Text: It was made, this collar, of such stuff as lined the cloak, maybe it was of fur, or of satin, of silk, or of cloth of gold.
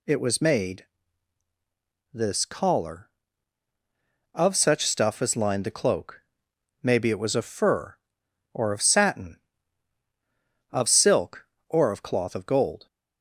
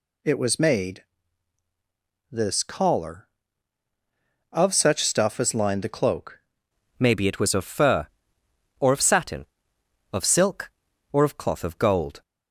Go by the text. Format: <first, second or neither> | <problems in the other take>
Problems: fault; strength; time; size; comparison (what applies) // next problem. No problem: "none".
first | changes voice at "maybe"; from 6.9 s on; 5.3 s long